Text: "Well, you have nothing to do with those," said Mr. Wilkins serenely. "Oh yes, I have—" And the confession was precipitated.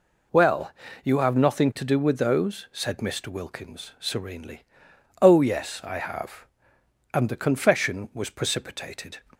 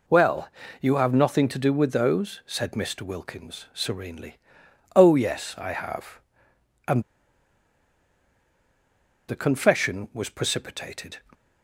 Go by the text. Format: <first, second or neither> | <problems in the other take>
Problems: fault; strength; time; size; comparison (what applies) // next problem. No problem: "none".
first | pauses between "And" and "the"; strong; at 7.0 s; 2.2 s long